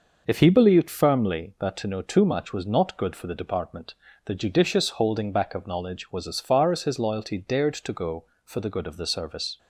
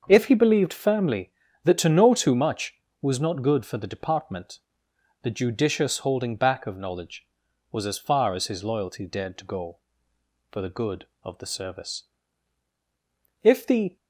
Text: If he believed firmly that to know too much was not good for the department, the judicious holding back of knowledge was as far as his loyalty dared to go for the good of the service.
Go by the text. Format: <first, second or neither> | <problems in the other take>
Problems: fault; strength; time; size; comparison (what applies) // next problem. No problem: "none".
first | starts louder than the rest; until 1.0 s; 6.5 dB // goes on to say "If the"; from 13.4 s on; 0.52 s long